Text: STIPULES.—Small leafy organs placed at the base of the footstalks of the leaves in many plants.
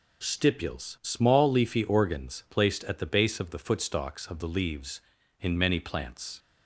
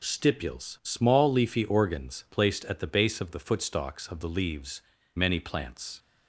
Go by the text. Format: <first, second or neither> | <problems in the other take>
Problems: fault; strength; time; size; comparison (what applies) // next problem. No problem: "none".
first | skips "in"; at 4.9 s